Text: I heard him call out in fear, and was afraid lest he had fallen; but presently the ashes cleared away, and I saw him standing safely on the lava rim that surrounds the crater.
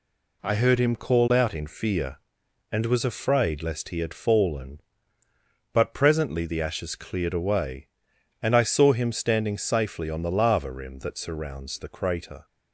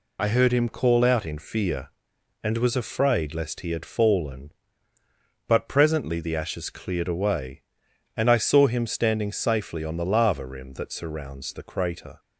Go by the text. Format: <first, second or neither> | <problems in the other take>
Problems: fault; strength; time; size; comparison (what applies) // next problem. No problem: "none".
first | loses the start of "I"; at 0.1 s; 50 ms